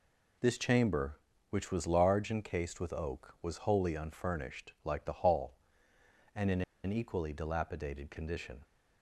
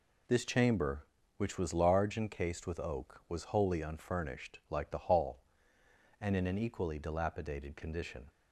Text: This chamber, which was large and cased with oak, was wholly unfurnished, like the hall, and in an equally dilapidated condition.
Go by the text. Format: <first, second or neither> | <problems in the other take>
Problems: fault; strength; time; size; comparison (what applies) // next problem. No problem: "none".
second | pauses between "in" and "an"; slight; at 6.6 s; 0.22 s long